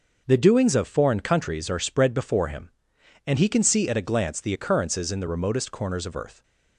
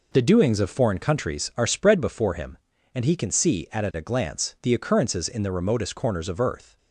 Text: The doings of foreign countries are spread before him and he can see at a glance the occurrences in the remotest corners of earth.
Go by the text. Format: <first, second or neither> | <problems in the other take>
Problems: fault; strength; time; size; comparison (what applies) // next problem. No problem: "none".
first | says "at" twice; at 3.8 s